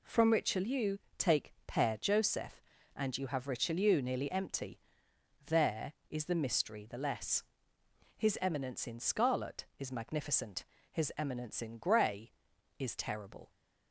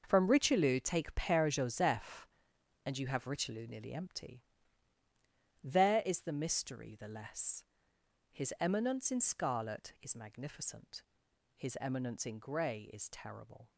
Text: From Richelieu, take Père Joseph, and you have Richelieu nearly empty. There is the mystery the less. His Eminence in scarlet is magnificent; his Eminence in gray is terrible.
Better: first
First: none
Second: gets quieter; strong; throughout; 11.5 dB

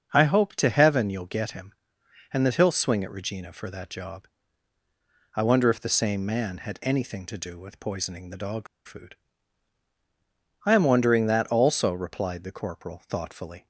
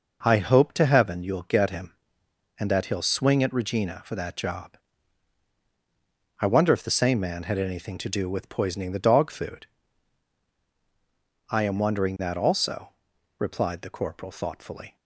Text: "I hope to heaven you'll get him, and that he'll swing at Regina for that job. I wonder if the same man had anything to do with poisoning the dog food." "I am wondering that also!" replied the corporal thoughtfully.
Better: second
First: starts louder than the rest; until 1.1 s; 6.5 dB // pauses between "dog" and "food"; slight; at 8.6 s; 0.20 s long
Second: none

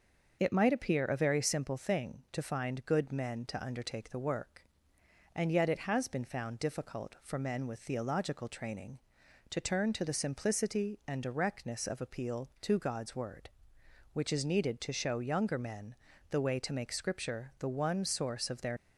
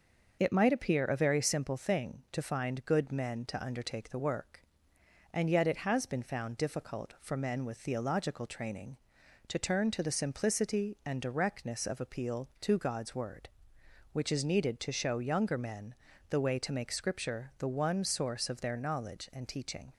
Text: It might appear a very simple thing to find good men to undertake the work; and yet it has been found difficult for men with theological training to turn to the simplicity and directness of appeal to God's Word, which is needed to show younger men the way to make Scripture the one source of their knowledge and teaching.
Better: second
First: starts louder than the rest; noticeable; until 1.4 s; 6 dB // pauses between "men" and "the"; at 15.9 s; 0.38 s long // stops before "knowledge and teaching"; at 18.7 s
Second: starts louder than the rest; noticeable; until 1.4 s; 6 dB // pauses between "men" and "the"; at 15.9 s; 0.38 s long

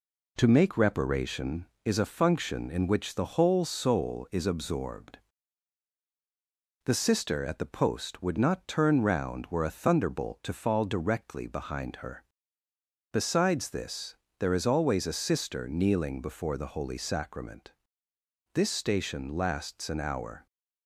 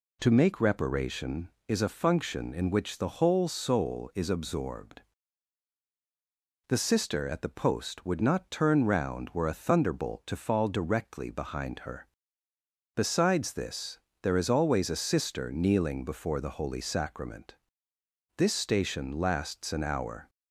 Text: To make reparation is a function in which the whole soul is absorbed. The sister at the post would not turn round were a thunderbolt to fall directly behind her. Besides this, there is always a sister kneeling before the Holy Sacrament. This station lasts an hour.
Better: second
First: gets quieter; slight; throughout; 3 dB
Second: none

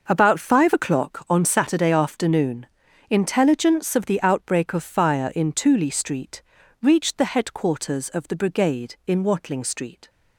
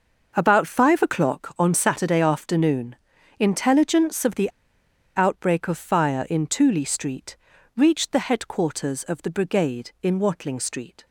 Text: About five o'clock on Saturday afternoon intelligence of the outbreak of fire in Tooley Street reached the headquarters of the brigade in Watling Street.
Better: first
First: pauses between "afternoon" and "intelligence"; at 2.6 s; 0.42 s long // pauses between "Street" and "reached"; at 6.4 s; 0.40 s long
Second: pauses between "afternoon" and "intelligence"; at 2.9 s; 0.42 s long // pauses between "the" and "outbreak"; noticeable; at 4.4 s; 0.66 s long // pauses between "Street" and "reached"; at 7.3 s; 0.40 s long

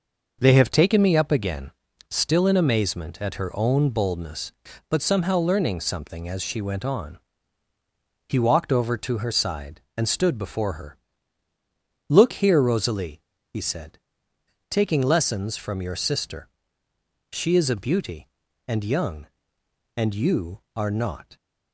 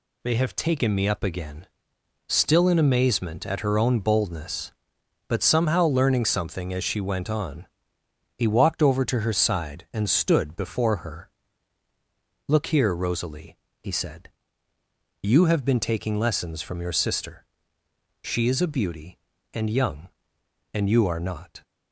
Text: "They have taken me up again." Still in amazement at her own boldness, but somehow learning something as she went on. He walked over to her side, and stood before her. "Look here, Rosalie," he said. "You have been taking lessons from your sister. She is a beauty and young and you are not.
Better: second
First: skips "You have been"; at 14.3 s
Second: none

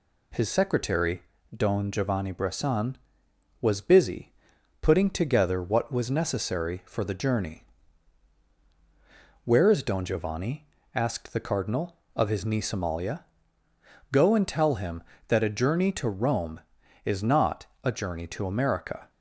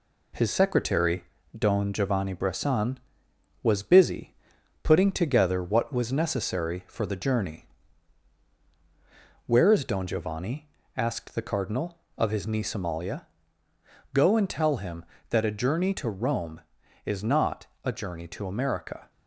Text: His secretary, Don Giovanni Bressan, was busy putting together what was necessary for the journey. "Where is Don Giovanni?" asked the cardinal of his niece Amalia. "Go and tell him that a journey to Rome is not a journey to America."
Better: first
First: pauses between "busy" and "putting"; noticeable; at 4.3 s; 0.48 s long // pauses between "not" and "a"; slight; at 17.6 s; 0.18 s long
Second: gets quieter; throughout; 4 dB // pauses between "busy" and "putting"; noticeable; at 4.3 s; 0.48 s long // pauses between "not" and "a"; slight; at 17.6 s; 0.18 s long

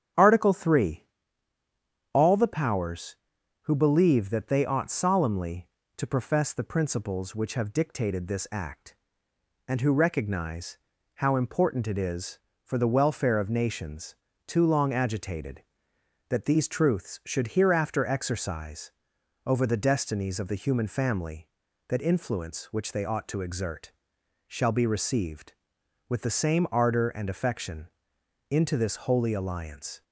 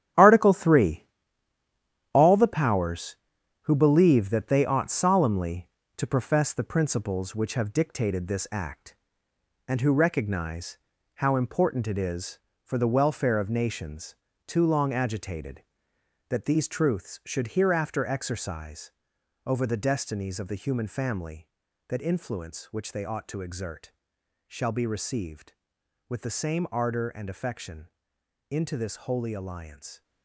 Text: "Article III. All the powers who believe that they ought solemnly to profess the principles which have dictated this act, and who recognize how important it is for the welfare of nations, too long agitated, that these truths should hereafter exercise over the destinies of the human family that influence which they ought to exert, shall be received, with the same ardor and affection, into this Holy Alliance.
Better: first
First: starts louder than the rest; strong; until 2.2 s; 9 dB // pauses between "recognize" and "how"; at 10.7 s; 0.38 s long // pauses between "exercise" and "over"; noticeable; at 18.9 s; 0.52 s long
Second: gets quieter; strong; throughout; 10 dB // starts louder than the rest; strong; until 2.2 s; 10.5 dB // pauses between "recognize" and "how"; at 10.7 s; 0.38 s long // pauses between "exercise" and "over"; noticeable; at 18.9 s; 0.52 s long

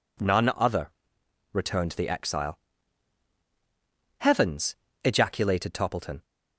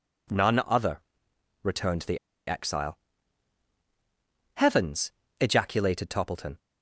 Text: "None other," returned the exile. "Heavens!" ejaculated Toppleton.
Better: first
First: none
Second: pauses between "the" and "exile"; slight; at 2.1 s; 0.29 s long

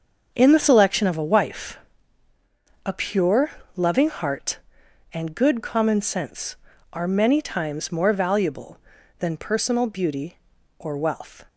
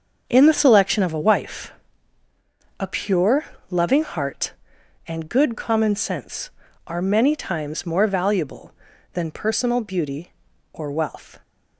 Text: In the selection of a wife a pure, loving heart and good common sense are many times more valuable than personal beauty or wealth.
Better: neither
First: starts louder than the rest; until 1.3 s; 7 dB // pauses between "wife" and "a"; at 1.7 s; 1.1 s long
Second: starts louder than the rest; until 1.2 s; 6.5 dB // pauses between "wife" and "a"; at 1.7 s; 1.1 s long

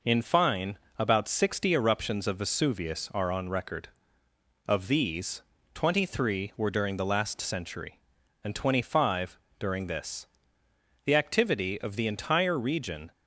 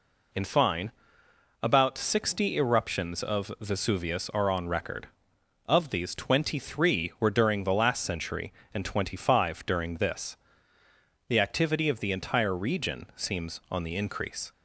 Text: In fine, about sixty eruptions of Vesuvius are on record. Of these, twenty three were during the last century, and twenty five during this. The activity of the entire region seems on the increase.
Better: second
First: pauses between "five" and "during"; slight; at 9.3 s; 0.22 s long // stops before "seems on the increase"; at 13.1 s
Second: none

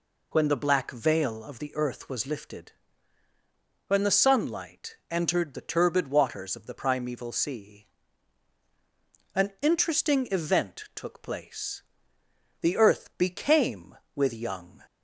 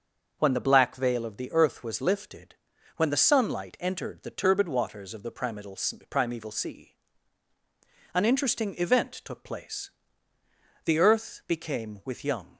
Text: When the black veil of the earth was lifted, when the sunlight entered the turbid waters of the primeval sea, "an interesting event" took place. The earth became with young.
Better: first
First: none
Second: says "primeval" twice; at 6.0 s

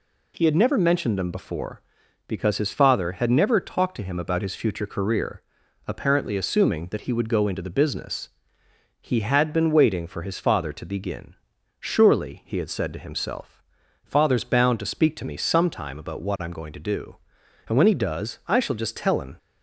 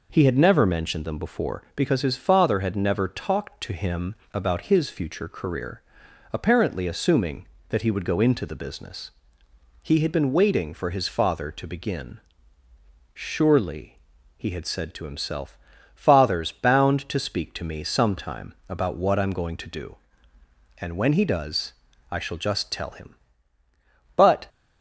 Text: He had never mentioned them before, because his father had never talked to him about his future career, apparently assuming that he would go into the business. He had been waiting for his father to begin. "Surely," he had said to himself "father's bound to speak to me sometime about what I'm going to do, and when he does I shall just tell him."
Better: first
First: pauses between "himself" and "father's"; at 13.6 s; 0.40 s long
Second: pauses between "him" and "about"; slight; at 4.1 s; 0.18 s long // pauses between "himself" and "father's"; slight; at 15.5 s; 0.34 s long // pauses between "does" and "I"; at 21.7 s; 0.38 s long // goes on to say "But"; slight; from 24.1 s on; 0.32 s long

